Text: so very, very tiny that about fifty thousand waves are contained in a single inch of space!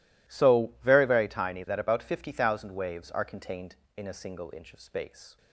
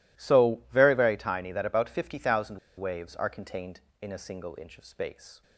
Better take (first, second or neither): first